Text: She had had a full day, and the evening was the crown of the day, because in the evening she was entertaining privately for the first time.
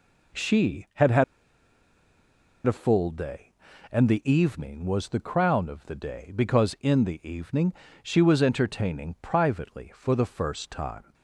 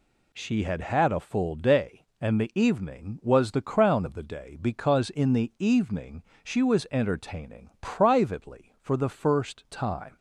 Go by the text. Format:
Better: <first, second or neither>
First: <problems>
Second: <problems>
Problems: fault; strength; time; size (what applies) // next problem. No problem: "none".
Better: second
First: pauses between "had" and "a"; strong; at 1.2 s; 1.4 s long // pauses between "evening" and "she"; slight; at 7.7 s; 0.30 s long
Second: pauses between "evening" and "she"; slight; at 6.2 s; 0.20 s long